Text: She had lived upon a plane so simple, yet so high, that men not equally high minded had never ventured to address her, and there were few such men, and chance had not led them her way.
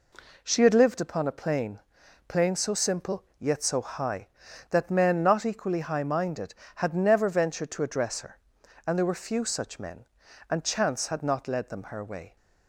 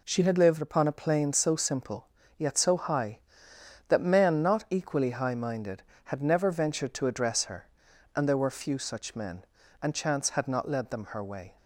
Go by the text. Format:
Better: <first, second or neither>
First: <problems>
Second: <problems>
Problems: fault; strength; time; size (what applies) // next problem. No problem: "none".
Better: second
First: says "plane" twice; at 2.2 s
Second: none